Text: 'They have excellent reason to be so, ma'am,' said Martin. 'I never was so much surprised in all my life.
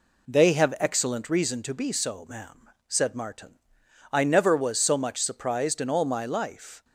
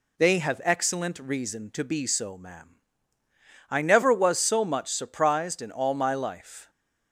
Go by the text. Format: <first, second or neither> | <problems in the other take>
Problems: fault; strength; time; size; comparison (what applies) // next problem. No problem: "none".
first | skips "said Martin"; at 3.2 s